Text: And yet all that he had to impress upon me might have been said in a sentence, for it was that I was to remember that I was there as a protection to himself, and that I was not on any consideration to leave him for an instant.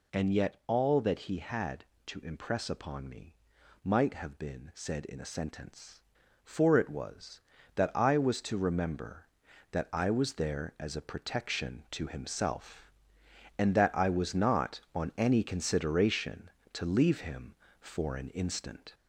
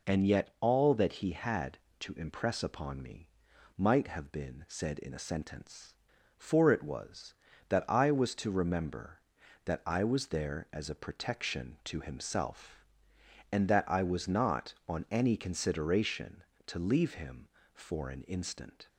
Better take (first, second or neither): second